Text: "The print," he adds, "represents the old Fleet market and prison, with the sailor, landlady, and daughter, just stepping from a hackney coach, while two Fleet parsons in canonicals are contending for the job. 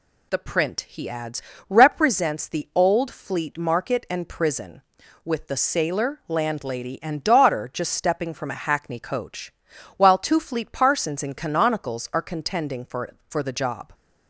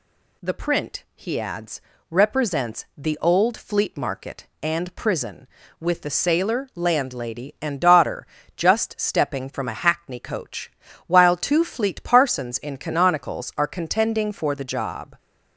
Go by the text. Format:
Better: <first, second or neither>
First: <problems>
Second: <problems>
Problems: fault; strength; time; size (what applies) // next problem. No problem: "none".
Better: second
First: says "for" twice; at 13.2 s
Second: none